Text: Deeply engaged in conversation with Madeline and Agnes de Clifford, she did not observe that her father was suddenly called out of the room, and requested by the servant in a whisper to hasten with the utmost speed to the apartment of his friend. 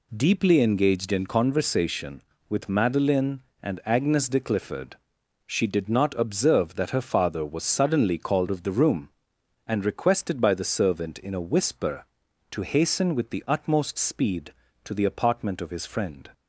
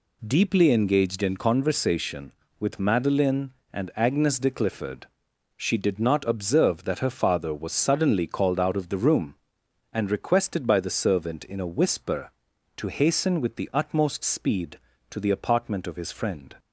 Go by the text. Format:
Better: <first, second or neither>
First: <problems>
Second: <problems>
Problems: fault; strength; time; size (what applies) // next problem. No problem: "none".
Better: second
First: skips "out"; at 8.4 s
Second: none